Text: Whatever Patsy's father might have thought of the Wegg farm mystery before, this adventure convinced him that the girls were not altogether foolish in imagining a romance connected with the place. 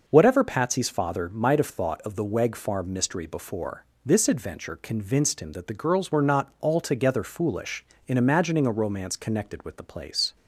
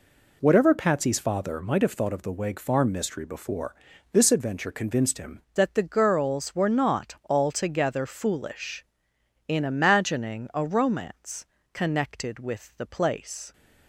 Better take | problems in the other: first | changes voice at "that"; from 5.5 s on; 8.0 s long // pauses between "romance" and "connected"; slight; at 11.4 s; 0.28 s long

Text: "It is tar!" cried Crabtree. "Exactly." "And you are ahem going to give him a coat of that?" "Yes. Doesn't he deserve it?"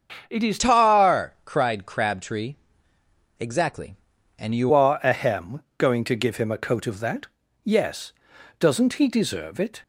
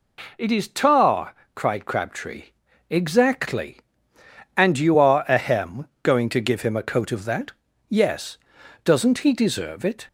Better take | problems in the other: second | starts louder than the rest; until 1.3 s; 6.5 dB // changes voice from "tar" to "you"; from 0.5 to 4.7 s; 4.2 s long // pauses between "ahem" and "going"; slight; at 5.6 s; 0.16 s long; slight in the second

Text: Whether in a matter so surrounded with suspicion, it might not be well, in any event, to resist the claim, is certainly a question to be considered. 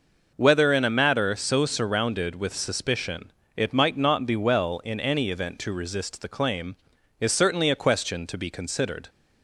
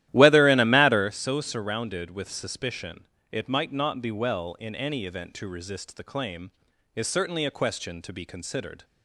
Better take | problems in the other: first | starts louder than the rest; strong; until 1.1 s; 13.5 dB

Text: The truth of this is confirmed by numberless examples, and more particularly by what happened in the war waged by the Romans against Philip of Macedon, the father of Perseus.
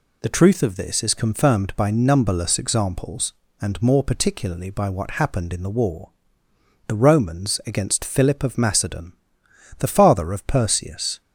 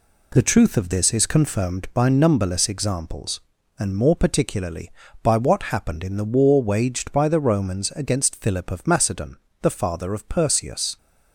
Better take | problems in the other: second | skips "waged by"; at 6.4 s

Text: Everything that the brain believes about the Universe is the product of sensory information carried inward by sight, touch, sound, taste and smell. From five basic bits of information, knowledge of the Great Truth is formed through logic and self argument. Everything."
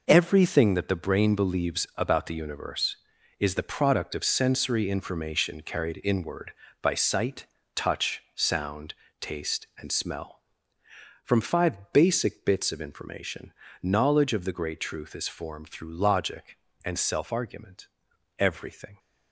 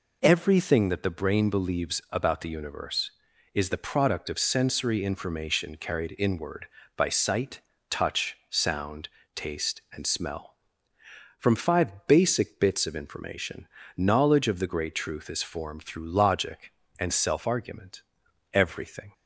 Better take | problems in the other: second | gets quieter; strong; throughout; 10 dB

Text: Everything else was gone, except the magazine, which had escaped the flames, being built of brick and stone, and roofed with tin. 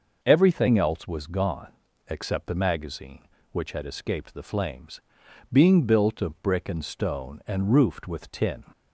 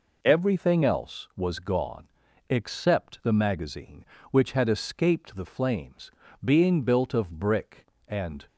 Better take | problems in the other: first | stops before "stone and roofed with tin"; at 8.4 s

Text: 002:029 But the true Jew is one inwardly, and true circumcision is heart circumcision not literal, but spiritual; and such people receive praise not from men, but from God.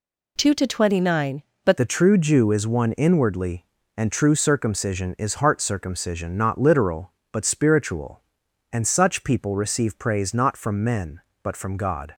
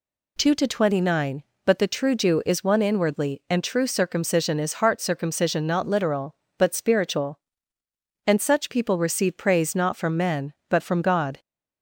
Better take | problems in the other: second | changes voice at "the"; from 1.7 s on; 10.4 s long

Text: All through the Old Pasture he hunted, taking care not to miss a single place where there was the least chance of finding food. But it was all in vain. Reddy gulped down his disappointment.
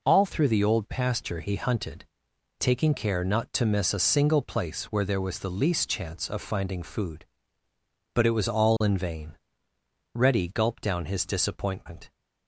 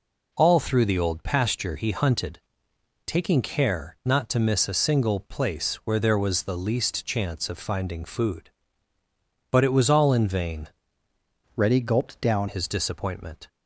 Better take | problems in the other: first | changes voice from "Reddy" to "down"; from 11.5 to 12.4 s; 0.9 s long

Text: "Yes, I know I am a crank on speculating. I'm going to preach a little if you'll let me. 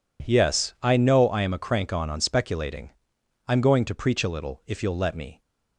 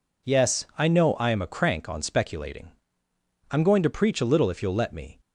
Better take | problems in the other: second | says "on" twice; at 2.1 s

